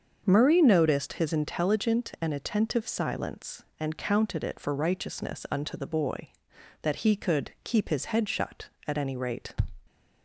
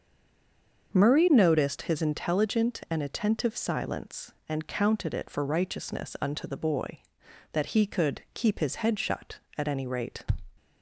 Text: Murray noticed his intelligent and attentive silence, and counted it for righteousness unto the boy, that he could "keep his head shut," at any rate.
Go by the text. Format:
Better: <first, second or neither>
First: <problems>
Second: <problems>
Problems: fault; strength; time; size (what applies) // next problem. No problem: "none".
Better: first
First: starts louder than the rest; until 1.2 s; 7 dB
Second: stays silent before the first word; slight; until 0.9 s; 0.9 s long // starts louder than the rest; until 1.9 s; 6.5 dB